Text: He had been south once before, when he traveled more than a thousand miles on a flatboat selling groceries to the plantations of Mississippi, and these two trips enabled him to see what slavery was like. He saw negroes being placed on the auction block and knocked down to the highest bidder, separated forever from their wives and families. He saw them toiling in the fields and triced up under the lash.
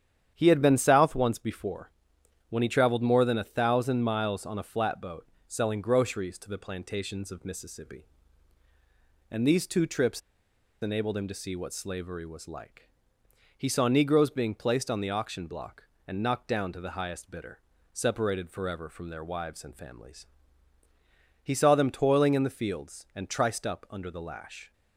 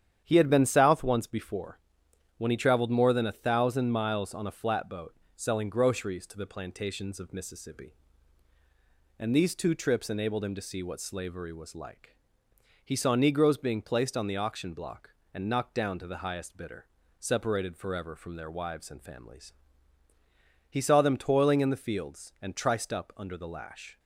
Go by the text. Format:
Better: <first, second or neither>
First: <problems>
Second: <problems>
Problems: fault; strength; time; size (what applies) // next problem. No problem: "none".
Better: second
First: starts louder than the rest; strong; until 1.3 s; 9.5 dB // pauses between "flatboat" and "selling"; slight; at 5.2 s; 0.22 s long // pauses between "trips" and "enabled"; noticeable; at 10.2 s; 0.61 s long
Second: starts louder than the rest; strong; until 1.2 s; 9 dB // pauses between "flatboat" and "selling"; slight; at 5.1 s; 0.22 s long